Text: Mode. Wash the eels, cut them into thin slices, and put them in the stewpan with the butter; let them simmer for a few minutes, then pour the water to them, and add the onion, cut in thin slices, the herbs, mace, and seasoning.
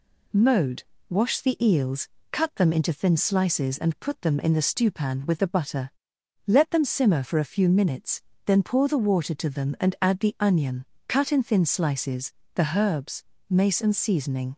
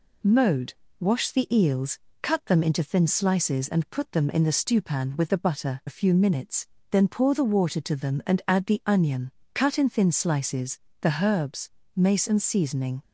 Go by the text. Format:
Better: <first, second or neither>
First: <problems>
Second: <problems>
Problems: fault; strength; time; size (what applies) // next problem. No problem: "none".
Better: first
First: none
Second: skips "let them simmer for"; at 5.8 s